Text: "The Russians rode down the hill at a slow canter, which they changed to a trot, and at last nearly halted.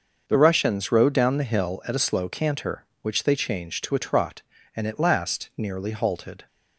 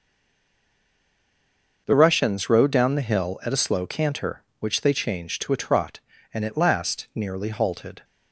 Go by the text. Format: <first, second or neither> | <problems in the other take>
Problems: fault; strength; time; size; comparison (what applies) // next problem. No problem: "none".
first | stays silent before the first word; noticeable; until 1.8 s; 1.8 s long // starts louder than the rest; until 2.8 s; 6 dB; also in the first